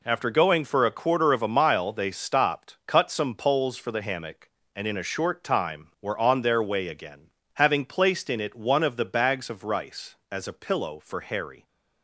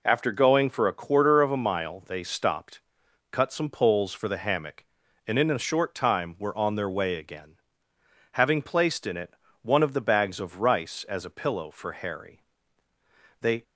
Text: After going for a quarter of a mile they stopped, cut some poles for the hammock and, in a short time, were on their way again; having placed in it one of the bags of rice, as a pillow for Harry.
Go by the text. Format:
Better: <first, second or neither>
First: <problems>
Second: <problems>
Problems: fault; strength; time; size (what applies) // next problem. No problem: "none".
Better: first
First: none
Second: pauses between "it" and "one"; slight; at 9.3 s; 0.28 s long // goes on to say "They"; slight; from 13.3 s on; 0.24 s long